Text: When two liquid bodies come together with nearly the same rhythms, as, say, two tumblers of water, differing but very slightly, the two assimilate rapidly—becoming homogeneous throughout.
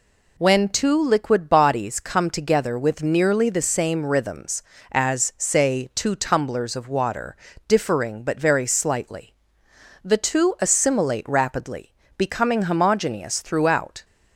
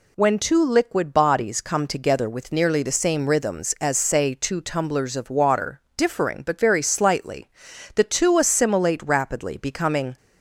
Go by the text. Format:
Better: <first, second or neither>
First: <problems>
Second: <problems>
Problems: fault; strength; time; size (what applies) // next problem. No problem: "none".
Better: first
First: none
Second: stops before "homogeneous throughout"; at 10.1 s